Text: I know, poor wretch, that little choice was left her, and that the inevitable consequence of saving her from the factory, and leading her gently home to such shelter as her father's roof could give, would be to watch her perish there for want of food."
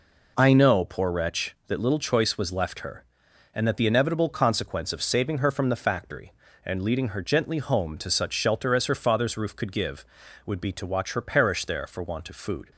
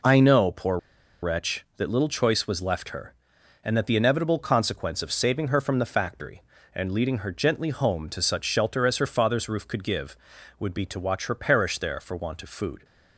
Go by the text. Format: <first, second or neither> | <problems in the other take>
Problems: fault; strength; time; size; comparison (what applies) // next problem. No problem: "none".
first | pauses between "poor" and "wretch"; at 0.7 s; 0.43 s long